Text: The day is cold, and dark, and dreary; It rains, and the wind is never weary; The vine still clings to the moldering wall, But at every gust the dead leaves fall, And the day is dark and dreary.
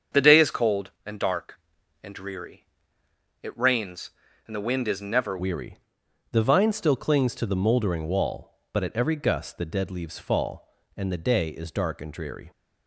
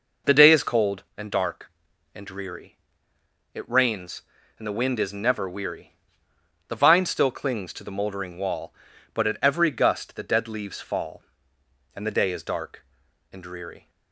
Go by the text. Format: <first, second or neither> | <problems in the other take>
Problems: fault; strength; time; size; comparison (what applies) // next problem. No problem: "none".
second | starts louder than the rest; strong; until 1.3 s; 7.5 dB // changes voice at "weary"; from 5.3 s on; 7.2 s long